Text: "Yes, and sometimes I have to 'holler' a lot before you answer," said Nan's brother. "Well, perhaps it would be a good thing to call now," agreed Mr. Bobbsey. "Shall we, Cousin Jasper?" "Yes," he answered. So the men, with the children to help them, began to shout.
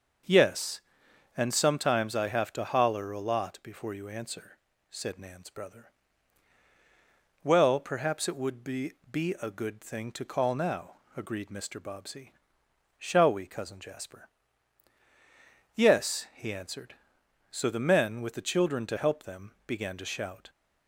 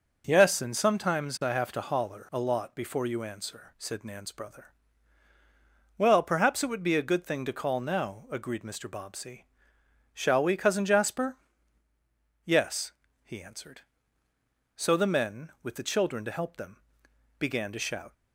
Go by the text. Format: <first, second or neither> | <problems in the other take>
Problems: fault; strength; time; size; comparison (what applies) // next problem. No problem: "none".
second | starts louder than the rest; until 1.8 s; 6.5 dB // says "be" twice; at 9.1 s